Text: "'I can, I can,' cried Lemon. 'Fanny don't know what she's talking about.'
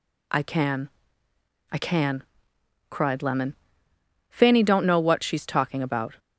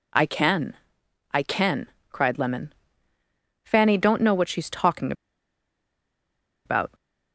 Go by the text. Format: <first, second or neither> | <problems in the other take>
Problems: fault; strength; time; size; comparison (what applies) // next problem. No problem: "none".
first | pauses between "talking" and "about"; strong; at 5.1 s; 1.5 s long